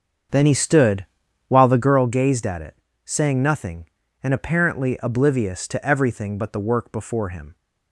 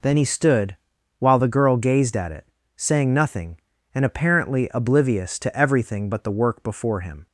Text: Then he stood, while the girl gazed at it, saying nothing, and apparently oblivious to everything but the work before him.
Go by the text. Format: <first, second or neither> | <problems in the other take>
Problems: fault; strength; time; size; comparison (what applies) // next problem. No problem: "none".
second | starts louder than the rest; strong; until 2.0 s; 7 dB